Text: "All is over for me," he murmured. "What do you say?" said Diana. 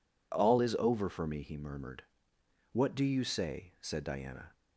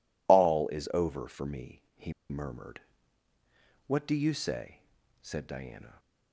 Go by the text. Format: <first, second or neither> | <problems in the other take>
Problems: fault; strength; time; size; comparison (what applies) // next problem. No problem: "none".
first | pauses between "he" and "murmured"; slight; at 2.1 s; 0.17 s long